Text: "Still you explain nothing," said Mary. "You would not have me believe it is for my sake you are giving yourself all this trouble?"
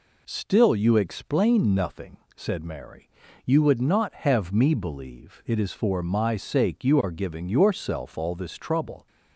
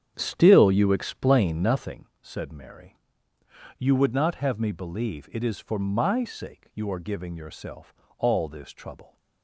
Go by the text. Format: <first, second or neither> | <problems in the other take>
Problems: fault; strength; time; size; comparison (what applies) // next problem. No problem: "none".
first | starts louder than the rest; strong; until 2.1 s; 8.5 dB // pauses between "yourself" and "all"; slight; at 7.9 s; 0.24 s long